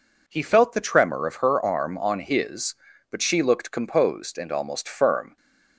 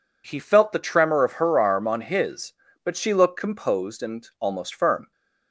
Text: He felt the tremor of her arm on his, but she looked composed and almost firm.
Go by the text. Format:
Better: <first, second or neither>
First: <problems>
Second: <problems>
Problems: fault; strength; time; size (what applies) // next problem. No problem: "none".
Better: neither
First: none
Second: none